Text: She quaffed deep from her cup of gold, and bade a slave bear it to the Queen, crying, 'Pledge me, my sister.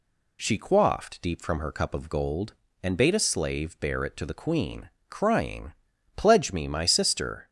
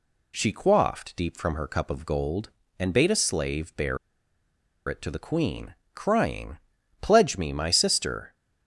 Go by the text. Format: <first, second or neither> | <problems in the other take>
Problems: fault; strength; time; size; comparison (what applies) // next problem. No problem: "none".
first | pauses between "bear" and "it"; noticeable; at 3.9 s; 0.91 s long